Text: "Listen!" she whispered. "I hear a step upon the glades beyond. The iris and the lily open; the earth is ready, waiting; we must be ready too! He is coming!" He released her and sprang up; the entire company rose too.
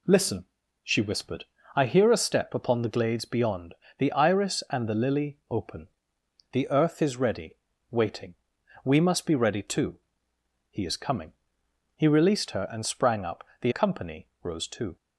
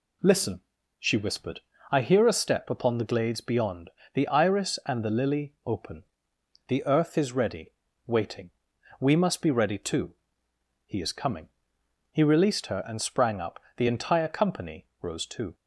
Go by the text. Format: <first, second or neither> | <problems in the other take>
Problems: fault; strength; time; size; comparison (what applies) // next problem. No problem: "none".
second | skips "entire"; at 13.7 s